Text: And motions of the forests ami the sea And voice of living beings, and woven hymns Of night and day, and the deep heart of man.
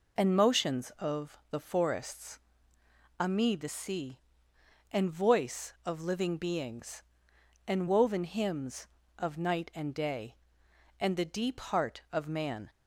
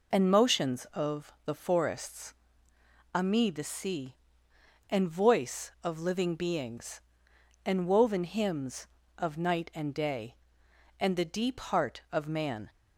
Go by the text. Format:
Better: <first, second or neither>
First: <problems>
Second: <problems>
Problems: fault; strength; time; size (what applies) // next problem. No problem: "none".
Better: neither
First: pauses between "forests" and "ami"; noticeable; at 2.3 s; 0.80 s long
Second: pauses between "forests" and "ami"; noticeable; at 2.3 s; 0.80 s long